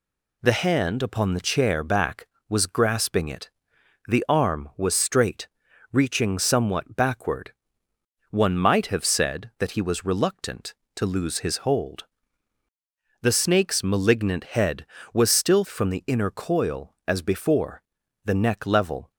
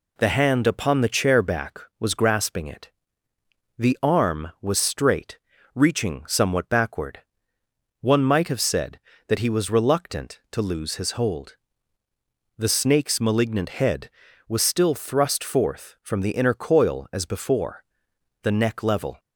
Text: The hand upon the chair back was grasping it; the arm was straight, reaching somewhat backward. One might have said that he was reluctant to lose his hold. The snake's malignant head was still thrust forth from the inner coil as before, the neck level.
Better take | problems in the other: second | skips "thrust forth"; at 15.6 s

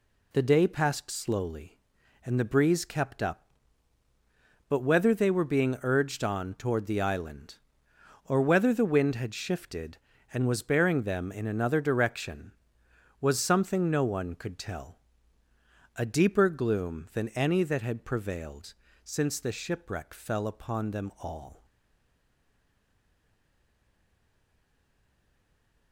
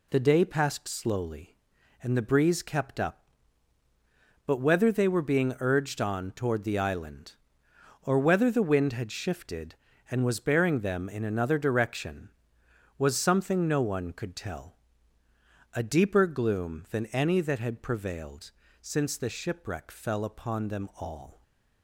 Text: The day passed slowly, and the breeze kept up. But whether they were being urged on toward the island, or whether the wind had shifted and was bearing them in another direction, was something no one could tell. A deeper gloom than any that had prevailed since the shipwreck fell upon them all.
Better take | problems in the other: second | pauses between "prevailed" and "since"; slight; at 18.7 s; 0.30 s long; slight in the second // stays silent after the last word; strong; from 21.6 s on; 4.3 s long

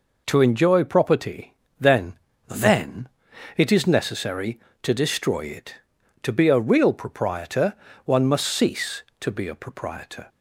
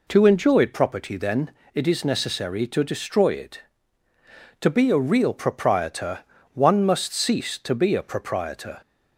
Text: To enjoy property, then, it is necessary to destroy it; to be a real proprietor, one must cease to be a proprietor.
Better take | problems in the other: second | says "then" twice; at 2.4 s

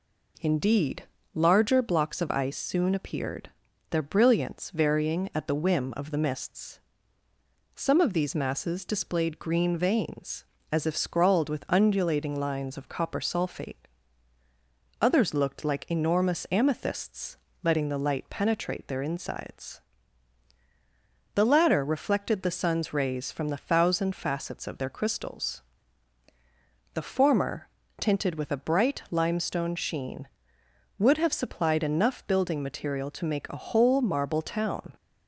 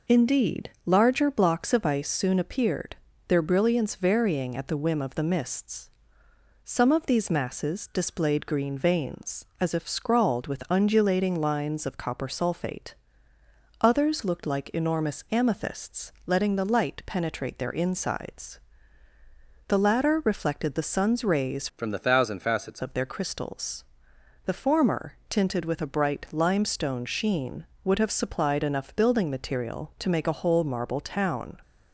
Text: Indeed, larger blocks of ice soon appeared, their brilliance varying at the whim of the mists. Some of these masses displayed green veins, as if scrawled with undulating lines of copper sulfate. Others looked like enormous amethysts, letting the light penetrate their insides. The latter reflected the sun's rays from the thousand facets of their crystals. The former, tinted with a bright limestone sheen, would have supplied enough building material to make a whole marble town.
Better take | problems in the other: first | changes voice from "from" to "facets"; from 21.7 to 22.8 s; 1.1 s long

